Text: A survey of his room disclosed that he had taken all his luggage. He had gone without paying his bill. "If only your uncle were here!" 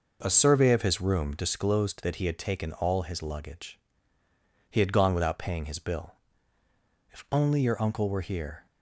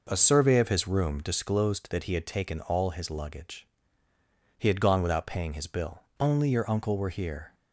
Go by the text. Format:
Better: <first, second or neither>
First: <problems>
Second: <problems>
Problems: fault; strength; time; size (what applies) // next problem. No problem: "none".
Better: first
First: none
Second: skips "If"; at 6.0 s